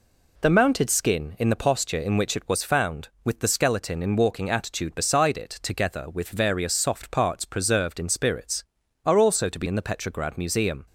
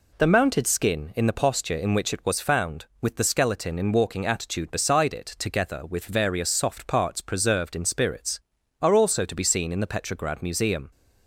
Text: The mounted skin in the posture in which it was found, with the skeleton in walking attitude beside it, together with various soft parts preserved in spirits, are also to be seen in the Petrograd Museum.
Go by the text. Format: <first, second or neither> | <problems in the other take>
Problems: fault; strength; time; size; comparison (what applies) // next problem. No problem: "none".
second | skips "seen"; at 9.6 s